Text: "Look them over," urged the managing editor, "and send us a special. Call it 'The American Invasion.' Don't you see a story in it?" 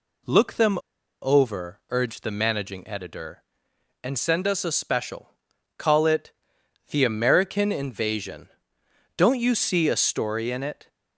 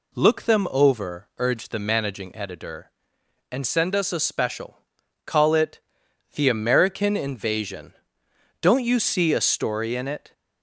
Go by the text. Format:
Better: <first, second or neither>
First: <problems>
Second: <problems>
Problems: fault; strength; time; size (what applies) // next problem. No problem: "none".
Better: second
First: pauses between "them" and "over"; at 0.7 s; 0.42 s long // pauses between "it" and "The"; noticeable; at 6.3 s; 0.56 s long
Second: pauses between "it" and "The"; noticeable; at 5.8 s; 0.52 s long